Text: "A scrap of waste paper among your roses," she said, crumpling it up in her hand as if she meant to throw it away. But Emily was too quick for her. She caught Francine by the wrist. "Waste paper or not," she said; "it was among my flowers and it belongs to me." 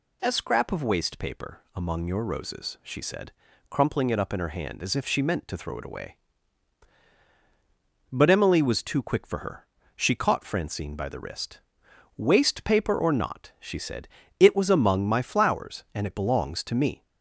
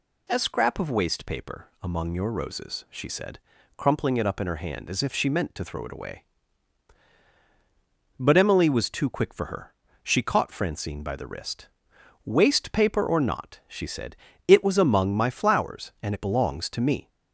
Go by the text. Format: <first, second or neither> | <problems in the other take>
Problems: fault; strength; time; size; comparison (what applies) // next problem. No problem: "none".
neither | none